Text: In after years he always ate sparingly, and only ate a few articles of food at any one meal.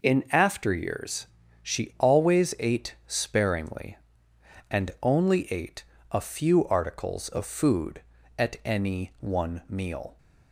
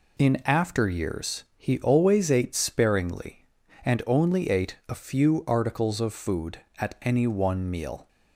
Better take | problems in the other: second | says "she" for "he"; at 1.6 s // pauses between "ate" and "a"; slight; at 5.8 s; 0.26 s long

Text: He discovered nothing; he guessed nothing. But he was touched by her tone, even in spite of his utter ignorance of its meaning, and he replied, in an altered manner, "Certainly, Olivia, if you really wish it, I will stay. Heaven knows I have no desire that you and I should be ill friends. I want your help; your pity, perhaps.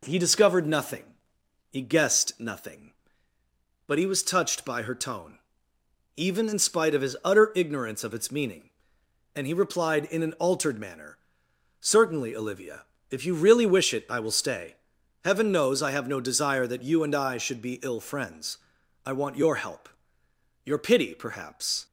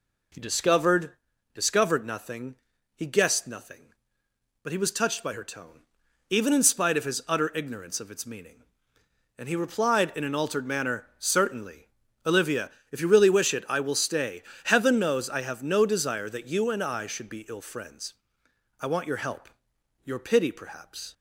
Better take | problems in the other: first | says "discovered" twice; at 1.5 s

